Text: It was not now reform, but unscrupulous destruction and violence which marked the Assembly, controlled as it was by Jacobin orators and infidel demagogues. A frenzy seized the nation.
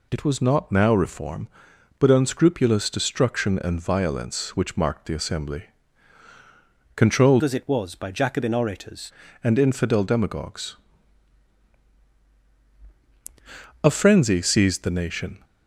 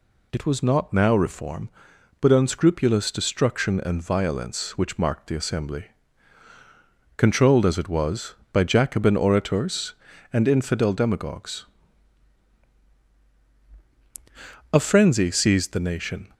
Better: second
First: changes voice from "as" to "orators"; from 7.4 to 9.1 s; 1.7 s long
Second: none

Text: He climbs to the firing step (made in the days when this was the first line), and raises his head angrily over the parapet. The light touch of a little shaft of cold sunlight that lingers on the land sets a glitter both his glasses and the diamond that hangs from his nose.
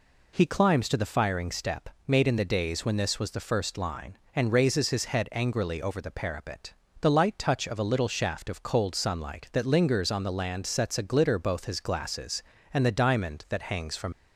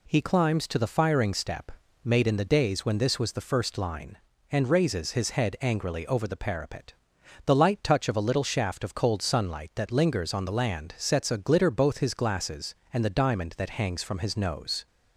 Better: second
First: stops before "his nose"; at 14.1 s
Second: none

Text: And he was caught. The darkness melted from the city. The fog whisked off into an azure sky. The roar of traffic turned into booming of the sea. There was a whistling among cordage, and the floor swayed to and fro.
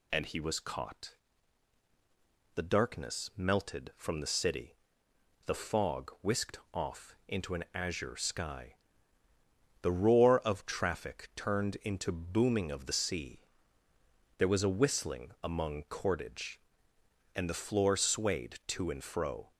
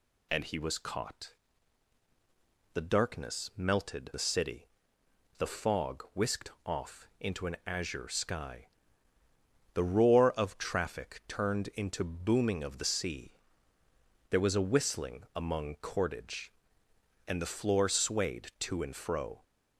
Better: first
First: none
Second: skips "from"; at 4.1 s

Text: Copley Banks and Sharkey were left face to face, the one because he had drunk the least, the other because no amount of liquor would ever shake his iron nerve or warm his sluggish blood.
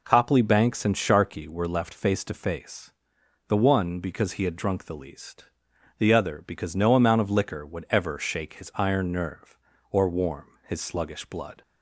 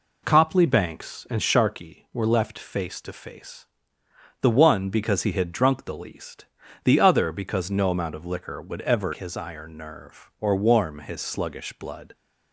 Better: first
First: none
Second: skips "shake"; at 9.1 s

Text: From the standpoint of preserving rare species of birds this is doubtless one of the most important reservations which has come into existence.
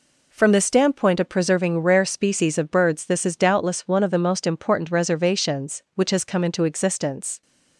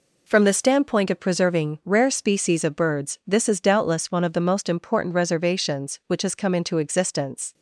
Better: neither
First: none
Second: none

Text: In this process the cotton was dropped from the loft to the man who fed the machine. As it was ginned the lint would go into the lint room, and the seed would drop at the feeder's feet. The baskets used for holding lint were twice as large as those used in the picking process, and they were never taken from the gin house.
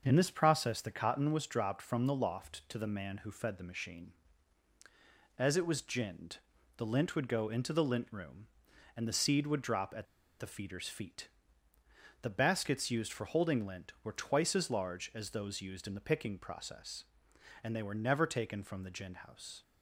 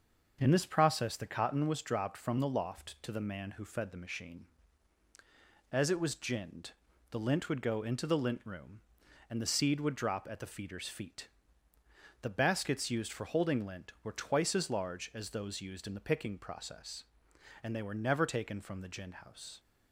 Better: second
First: starts louder than the rest; until 1.0 s; 6.5 dB // pauses between "ginned" and "the"; at 6.3 s; 0.38 s long // pauses between "at" and "the"; slight; at 10.0 s; 0.34 s long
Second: starts louder than the rest; until 1.4 s; 6.5 dB // pauses between "ginned" and "the"; at 6.7 s; 0.38 s long

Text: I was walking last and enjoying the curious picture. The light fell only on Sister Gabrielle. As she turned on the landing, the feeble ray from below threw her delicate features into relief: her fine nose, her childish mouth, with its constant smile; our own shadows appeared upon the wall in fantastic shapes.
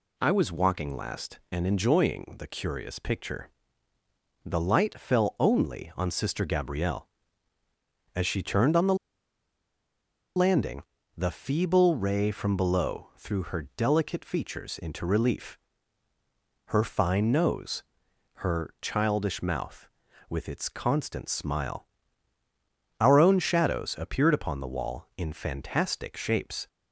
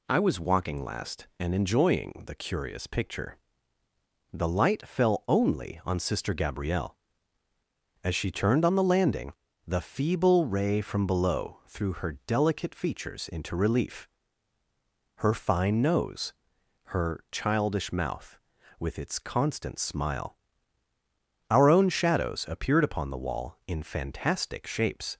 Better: second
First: pauses between "the" and "landing"; strong; at 8.9 s; 1.4 s long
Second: none

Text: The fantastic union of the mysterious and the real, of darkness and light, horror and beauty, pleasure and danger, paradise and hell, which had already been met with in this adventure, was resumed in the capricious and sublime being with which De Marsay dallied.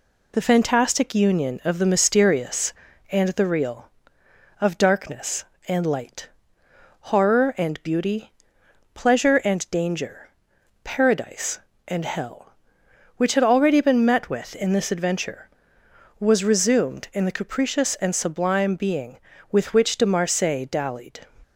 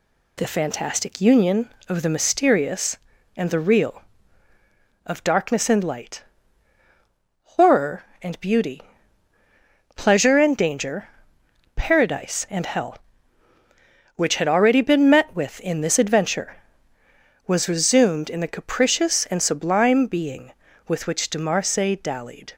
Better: neither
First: none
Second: none

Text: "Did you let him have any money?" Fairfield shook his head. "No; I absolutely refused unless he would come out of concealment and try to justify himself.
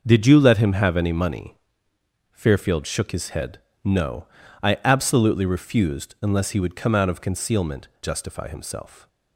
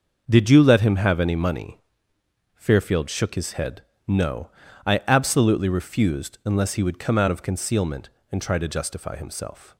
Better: second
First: starts louder than the rest; until 1.0 s; 6 dB // skips "and try to"; at 7.9 s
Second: starts louder than the rest; until 1.2 s; 6.5 dB

